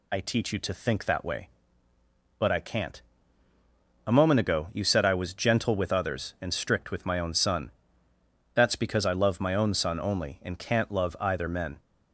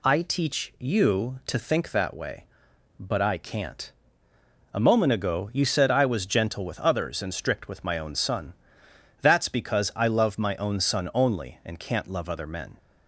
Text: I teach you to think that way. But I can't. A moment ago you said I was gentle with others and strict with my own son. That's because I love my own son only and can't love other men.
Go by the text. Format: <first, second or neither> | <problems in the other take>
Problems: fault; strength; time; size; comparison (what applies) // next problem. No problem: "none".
second | says "either" for "other"; at 11.1 s